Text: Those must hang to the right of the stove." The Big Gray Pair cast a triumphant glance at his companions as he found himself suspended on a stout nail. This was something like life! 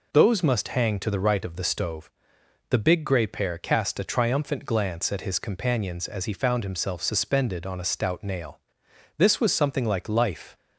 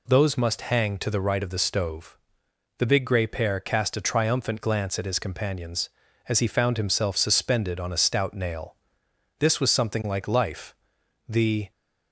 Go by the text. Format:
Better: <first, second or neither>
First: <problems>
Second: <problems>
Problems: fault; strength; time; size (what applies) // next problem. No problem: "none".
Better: first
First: none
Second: goes on to say "The"; slight; from 11.2 s on; 0.44 s long